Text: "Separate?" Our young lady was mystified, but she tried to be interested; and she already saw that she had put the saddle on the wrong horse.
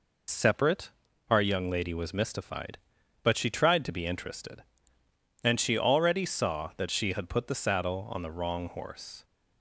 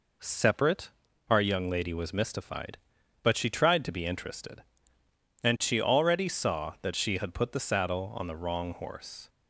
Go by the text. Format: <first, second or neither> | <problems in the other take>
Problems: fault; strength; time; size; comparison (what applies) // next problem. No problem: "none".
second | loses the start of "Separate"; at 0.2 s; 65 ms